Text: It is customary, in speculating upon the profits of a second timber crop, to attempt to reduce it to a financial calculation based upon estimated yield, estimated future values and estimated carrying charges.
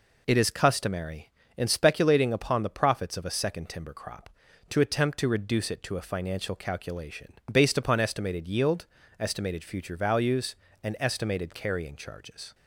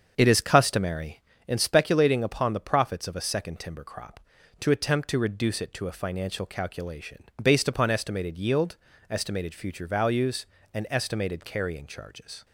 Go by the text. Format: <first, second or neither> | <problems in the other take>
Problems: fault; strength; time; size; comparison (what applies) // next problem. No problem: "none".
first | starts louder than the rest; until 1.4 s; 7 dB // pauses between "calculation" and "based"; slight; at 7.2 s; 0.18 s long; slight in the first